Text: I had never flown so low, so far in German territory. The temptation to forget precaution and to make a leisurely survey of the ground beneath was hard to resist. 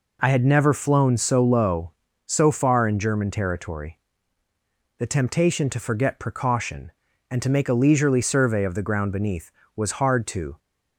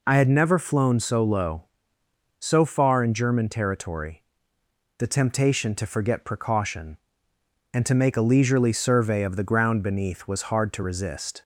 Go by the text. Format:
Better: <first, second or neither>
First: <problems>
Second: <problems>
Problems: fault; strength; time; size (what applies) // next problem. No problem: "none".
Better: second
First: stops before "resist"; at 10.5 s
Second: none